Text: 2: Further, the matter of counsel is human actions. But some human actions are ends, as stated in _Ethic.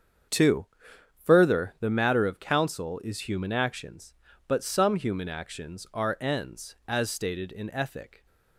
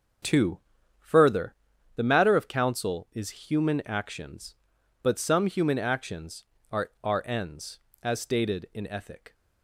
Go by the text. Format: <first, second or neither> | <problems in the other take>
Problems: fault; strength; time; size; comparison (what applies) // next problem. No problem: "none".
first | starts louder than the rest; until 2.0 s; 6 dB; strong in the first // says "are" twice; at 7.0 s